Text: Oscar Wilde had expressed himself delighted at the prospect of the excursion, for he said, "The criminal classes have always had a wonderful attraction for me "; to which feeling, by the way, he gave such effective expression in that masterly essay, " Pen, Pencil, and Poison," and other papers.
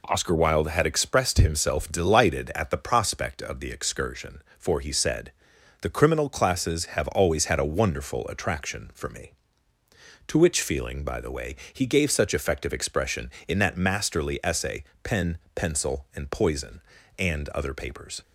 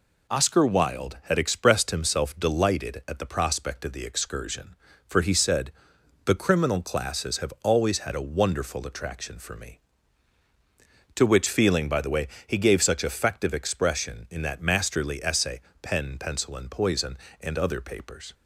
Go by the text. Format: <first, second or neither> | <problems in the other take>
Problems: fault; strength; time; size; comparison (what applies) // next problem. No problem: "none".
neither | none